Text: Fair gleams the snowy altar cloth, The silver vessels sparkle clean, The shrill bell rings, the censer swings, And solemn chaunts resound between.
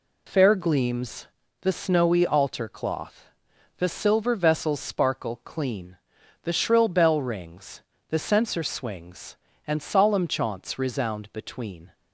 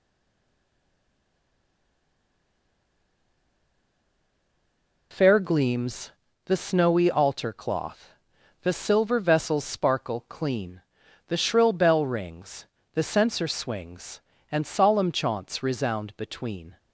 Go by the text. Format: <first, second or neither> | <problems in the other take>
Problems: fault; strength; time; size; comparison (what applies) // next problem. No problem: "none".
first | stays silent before the first word; strong; until 5.1 s; 5.1 s long // pauses between "gleams" and "the"; slight; at 6.0 s; 0.36 s long; slight in the first